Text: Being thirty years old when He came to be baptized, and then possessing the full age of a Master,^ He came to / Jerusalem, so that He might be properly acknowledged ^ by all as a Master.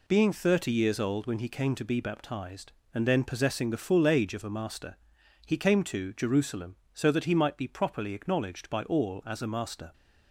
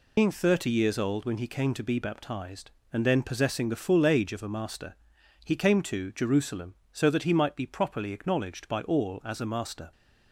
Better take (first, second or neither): first